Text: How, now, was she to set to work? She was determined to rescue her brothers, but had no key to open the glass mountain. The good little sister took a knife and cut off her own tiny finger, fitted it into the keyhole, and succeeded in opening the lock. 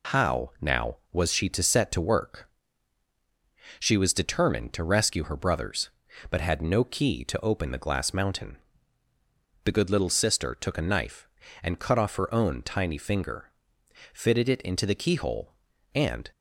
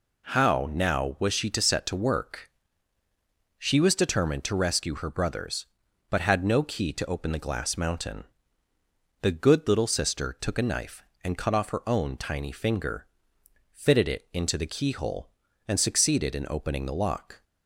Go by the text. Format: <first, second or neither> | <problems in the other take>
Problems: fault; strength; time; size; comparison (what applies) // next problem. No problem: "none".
second | stops before "succeeded in opening the lock"; at 16.3 s